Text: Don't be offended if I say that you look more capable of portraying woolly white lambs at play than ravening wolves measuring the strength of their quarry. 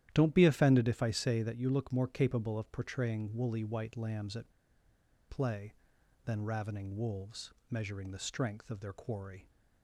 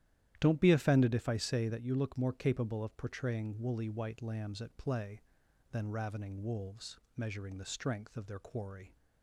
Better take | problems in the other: second | starts louder than the rest; strong; until 1.1 s; 12 dB; strong in the second // pauses between "at" and "play"; noticeable; at 4.5 s; 0.77 s long // pauses between "wolves" and "measuring"; slight; at 7.5 s; 0.18 s long; slight in the second

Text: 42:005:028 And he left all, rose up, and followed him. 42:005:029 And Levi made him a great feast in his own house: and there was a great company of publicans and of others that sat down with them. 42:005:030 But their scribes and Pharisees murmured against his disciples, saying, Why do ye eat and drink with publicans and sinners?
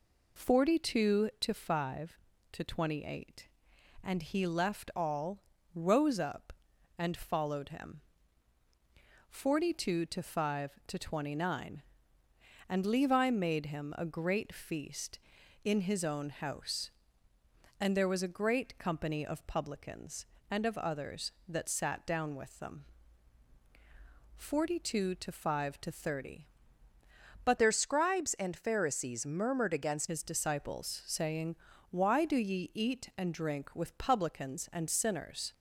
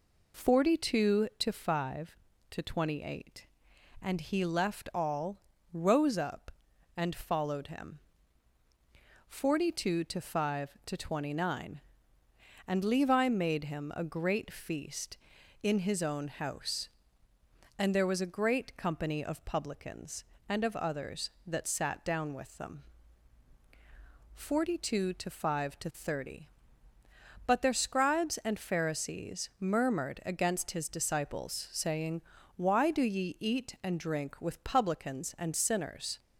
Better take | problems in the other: second | changes voice from "their" to "against"; from 27.5 to 30.0 s; 2.5 s long

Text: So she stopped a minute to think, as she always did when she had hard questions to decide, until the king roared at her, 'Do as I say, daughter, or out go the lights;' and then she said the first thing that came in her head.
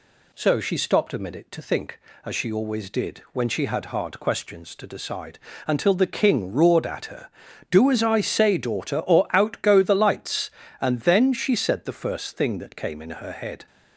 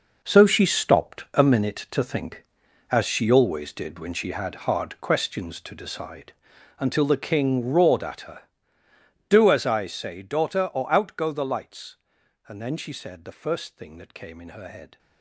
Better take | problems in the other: first | gets quieter; strong; throughout; 12 dB

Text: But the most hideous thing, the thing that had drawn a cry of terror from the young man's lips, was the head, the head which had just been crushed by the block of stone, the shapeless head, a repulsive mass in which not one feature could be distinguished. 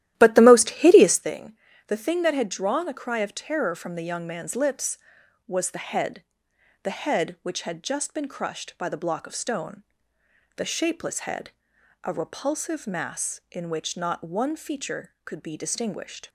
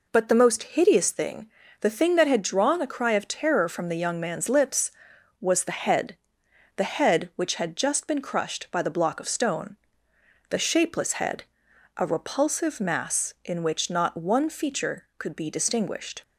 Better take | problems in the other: second | starts louder than the rest; strong; until 1.4 s; 13 dB

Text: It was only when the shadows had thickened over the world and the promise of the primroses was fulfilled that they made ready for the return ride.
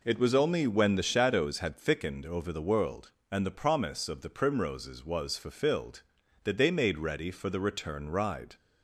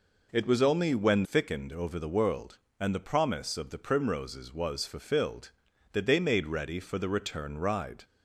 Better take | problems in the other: first | skips "the shadows had"; at 1.2 s

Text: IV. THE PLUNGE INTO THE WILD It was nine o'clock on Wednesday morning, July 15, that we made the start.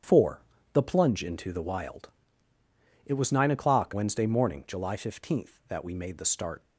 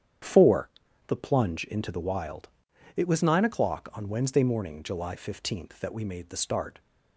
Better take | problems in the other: second | starts louder than the rest; strong; until 1.3 s; 8.5 dB; strong in the second // pauses between "WILD" and "It"; noticeable; at 2.1 s; 0.96 s long; noticeable in the second // skips "on"; at 3.9 s

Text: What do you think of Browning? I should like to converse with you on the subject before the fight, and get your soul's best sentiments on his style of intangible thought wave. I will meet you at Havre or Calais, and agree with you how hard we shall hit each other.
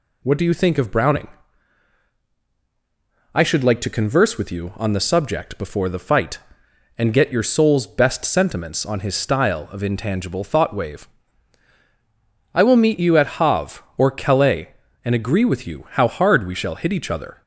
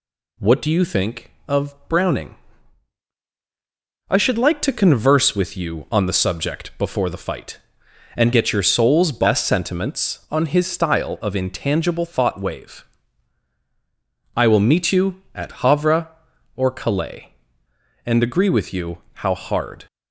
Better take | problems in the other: first | stops before "we shall hit each other"; at 19.8 s

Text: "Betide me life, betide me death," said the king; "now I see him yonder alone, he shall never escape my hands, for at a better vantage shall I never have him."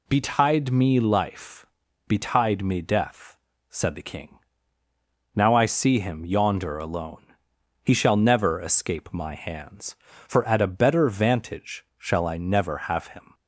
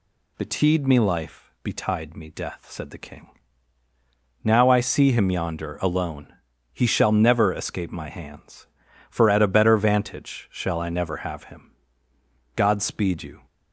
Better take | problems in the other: first | goes on to say "God speed you"; noticeable; from 12.5 s on; 0.88 s long

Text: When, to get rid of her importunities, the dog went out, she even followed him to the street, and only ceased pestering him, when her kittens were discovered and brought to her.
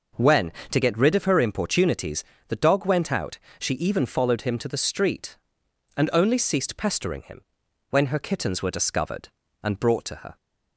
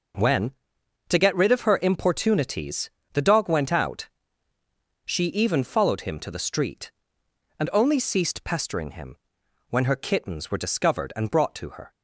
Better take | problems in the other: neither | none

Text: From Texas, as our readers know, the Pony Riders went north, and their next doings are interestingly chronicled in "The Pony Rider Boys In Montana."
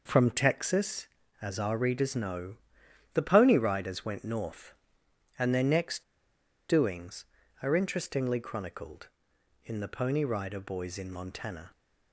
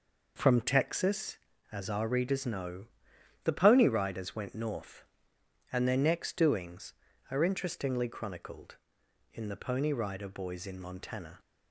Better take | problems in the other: second | pauses between "next" and "doings"; noticeable; at 6.0 s; 0.65 s long

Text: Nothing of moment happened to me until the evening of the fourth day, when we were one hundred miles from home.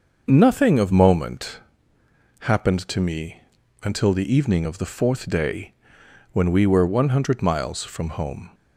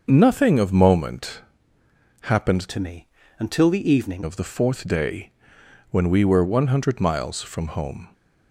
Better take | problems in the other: first | starts louder than the rest; until 1.0 s; 6.5 dB; also in the first // pauses between "moment" and "happened"; noticeable; at 1.4 s; 0.78 s long; noticeable in the first // changes voice from "to" to "evening"; from 2.7 to 4.2 s; 1.5 s long // pauses between "me" and "until"; slight; at 3.0 s; 0.34 s long; also in the first

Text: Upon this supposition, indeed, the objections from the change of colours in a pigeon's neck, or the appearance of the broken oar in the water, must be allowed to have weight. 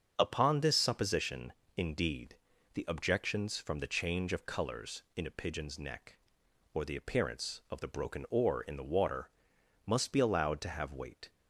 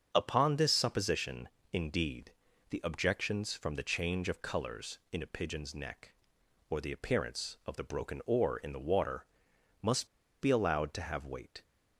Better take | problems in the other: first | starts louder than the rest; strong; until 1.1 s; 7 dB; strong in the first // pauses between "must" and "be"; slight; at 10.0 s; 0.33 s long

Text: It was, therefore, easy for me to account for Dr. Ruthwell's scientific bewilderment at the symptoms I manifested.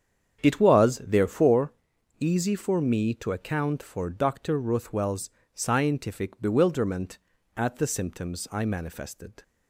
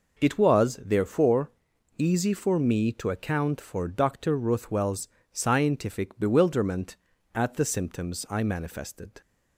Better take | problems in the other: second | starts louder than the rest; strong; until 1.7 s; 8 dB // pauses between "Ruthwell's" and "scientific"; slight; at 5.3 s; 0.22 s long; slight in the second

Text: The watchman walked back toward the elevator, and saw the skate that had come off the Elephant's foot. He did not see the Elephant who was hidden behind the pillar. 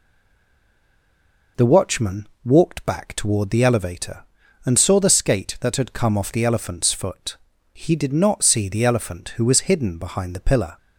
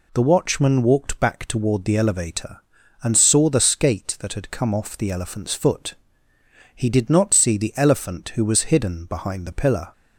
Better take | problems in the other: second | stays silent before the first word; noticeable; until 1.5 s; 1.5 s long // pauses between "watchman" and "walked"; slight; at 2.2 s; 0.18 s long

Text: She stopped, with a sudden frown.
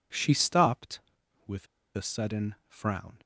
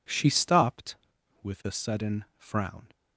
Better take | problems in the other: second | pauses between "with" and "a"; slight; at 1.6 s; 0.30 s long

